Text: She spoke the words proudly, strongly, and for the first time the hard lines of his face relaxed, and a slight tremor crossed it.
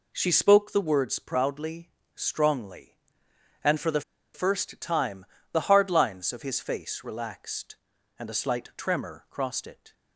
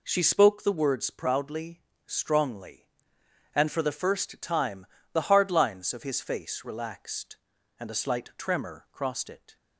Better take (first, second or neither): second